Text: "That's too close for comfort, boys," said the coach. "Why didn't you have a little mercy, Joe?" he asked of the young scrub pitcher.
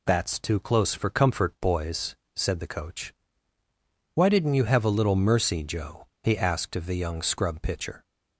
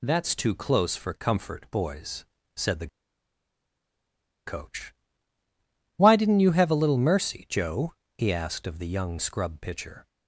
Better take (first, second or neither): first